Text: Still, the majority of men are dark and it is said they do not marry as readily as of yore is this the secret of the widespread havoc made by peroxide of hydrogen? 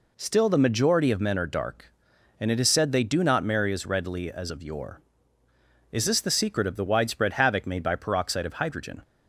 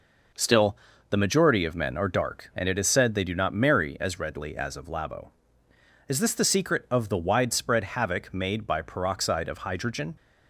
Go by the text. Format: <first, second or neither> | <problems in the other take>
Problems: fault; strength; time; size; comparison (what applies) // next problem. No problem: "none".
first | says "labo" for "yore"; at 4.8 s